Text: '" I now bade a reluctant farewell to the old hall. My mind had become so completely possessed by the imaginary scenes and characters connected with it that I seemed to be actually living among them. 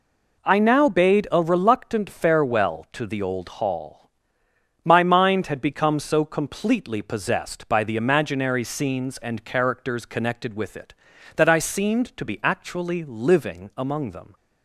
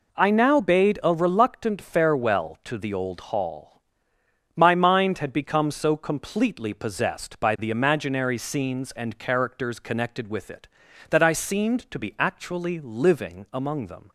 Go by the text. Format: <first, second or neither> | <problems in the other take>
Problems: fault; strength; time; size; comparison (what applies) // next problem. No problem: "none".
neither | none